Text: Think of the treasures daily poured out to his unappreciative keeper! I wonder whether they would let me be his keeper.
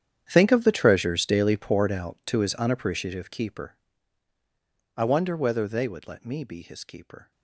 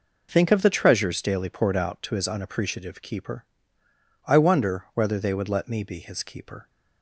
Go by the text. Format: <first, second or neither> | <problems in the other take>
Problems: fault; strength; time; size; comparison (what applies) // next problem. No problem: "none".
second | gets quieter; strong; throughout; 19 dB